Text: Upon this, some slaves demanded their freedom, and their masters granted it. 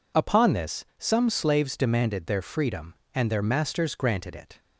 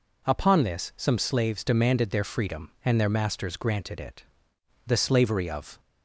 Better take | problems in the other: first | goes on to say "The slavery of"; noticeable; from 4.8 s on; 0.94 s long

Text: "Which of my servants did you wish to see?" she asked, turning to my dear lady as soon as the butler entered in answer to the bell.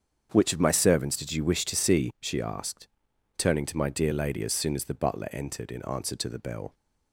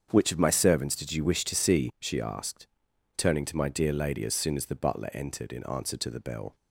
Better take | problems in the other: neither | starts louder than the rest; strong; the same in both

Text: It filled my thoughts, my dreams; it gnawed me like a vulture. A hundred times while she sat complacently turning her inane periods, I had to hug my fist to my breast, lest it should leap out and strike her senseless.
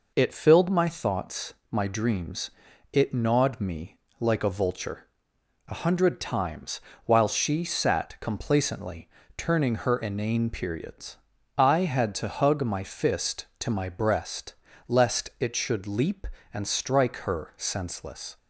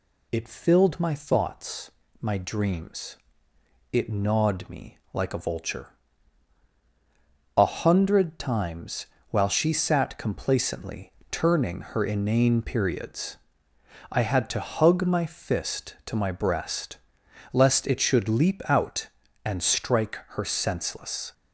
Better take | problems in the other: second | pauses between "me" and "like"; slight; at 3.9 s; 0.22 s long // pauses between "times" and "while"; slight; at 6.8 s; 0.26 s long; slight in the second // pauses between "complacently" and "turning"; slight; at 9.0 s; 0.28 s long; slight in the second // skips "out"; at 16.3 s

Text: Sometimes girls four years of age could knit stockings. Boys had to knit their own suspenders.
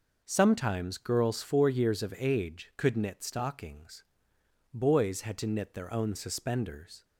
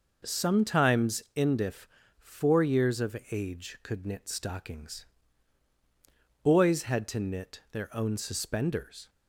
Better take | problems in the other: first | says "indif" for "girls"; at 1.3 s

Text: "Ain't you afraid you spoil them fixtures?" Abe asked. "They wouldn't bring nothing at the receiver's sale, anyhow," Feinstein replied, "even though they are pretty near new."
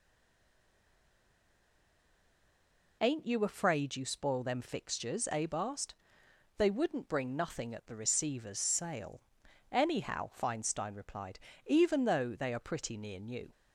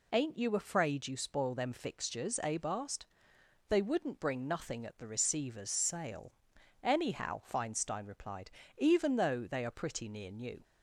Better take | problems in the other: second | stays silent before the first word; strong; until 3.0 s; 3.0 s long

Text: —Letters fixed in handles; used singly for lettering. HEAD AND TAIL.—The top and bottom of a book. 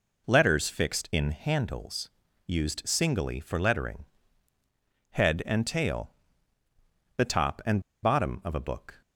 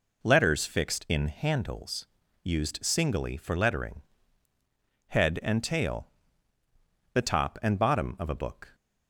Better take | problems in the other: second | pauses between "and" and "bottom"; slight; at 7.8 s; 0.22 s long

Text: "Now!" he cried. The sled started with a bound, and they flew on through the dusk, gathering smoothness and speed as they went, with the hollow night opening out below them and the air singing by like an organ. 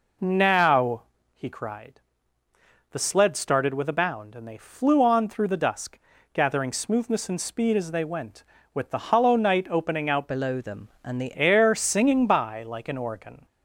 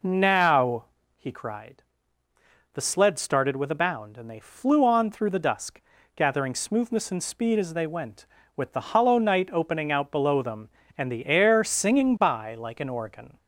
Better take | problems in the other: second | changes voice from "below" to "the"; from 10.2 to 11.3 s; 1.1 s long

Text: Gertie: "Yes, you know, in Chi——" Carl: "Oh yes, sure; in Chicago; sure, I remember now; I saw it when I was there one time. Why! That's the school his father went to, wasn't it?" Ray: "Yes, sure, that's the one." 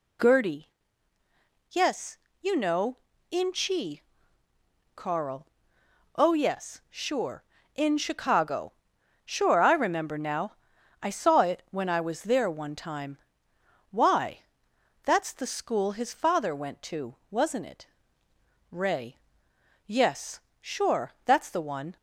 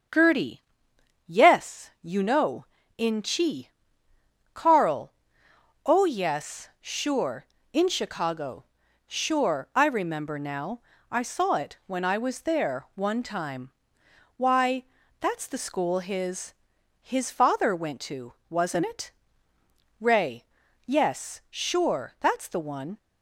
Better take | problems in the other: first | starts louder than the rest; strong; until 1.7 s; 7 dB // says "his" twice; at 17.0 s

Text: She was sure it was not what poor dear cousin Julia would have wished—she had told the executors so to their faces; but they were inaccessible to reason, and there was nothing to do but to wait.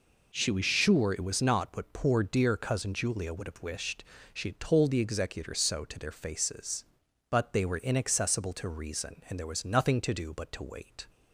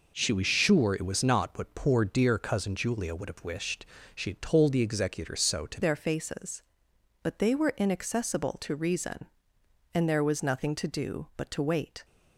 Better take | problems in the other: first | changes voice at "their"; from 5.8 s on; 6.2 s long

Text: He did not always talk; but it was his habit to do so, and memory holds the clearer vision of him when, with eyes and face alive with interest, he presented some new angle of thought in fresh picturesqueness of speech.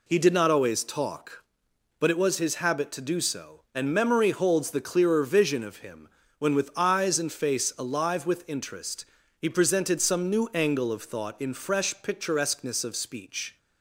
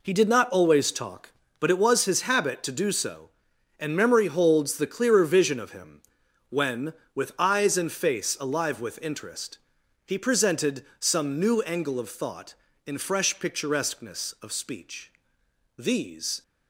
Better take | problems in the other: first | pauses between "him" and "when"; noticeable; at 6.0 s; 0.48 s long; slight in the first // goes on to say "These"; noticeable; from 15.7 s on; 0.66 s long

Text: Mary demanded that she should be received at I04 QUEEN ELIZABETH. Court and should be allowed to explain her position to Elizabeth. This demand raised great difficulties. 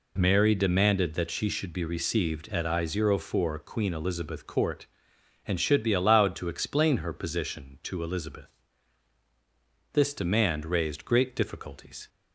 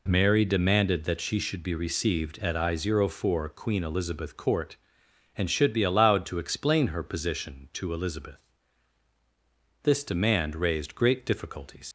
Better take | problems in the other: first | leaves "difficulties" unfinished; at 11.8 s; 75 ms

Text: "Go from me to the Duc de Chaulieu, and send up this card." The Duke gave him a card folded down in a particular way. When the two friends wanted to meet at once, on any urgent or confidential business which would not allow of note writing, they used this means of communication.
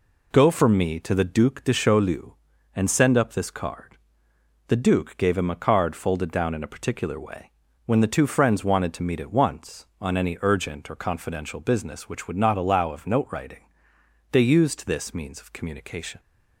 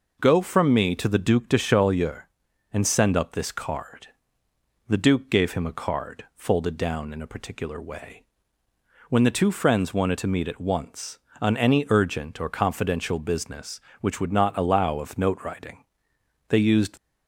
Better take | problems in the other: first | stops before "this means of communication"; at 16.9 s

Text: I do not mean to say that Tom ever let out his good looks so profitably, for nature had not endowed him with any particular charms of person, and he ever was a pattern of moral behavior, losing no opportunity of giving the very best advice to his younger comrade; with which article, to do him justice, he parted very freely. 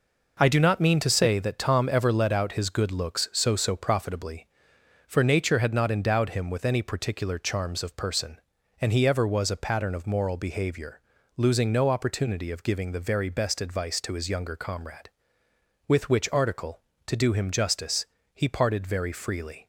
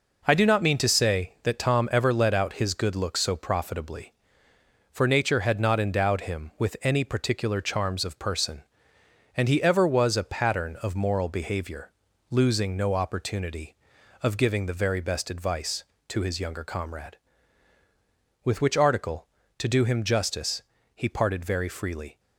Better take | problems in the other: second | says "so" twice; at 3.5 s

